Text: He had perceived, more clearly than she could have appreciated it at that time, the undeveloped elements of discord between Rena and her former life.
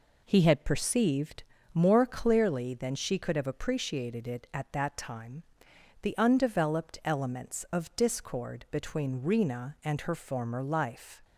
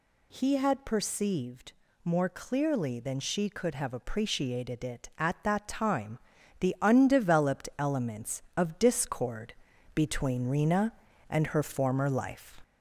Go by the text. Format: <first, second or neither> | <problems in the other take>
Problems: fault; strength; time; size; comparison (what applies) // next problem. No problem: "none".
first | gets louder; slight; throughout; 2.5 dB // pauses between "discord" and "between"; at 9.5 s; 0.42 s long